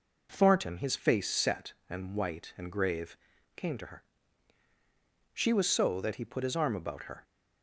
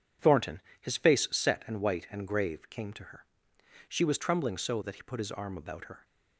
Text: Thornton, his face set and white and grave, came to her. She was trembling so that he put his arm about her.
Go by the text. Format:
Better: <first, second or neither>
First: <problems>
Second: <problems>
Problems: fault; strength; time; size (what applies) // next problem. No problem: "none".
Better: second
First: skips "trembling"; at 5.6 s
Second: none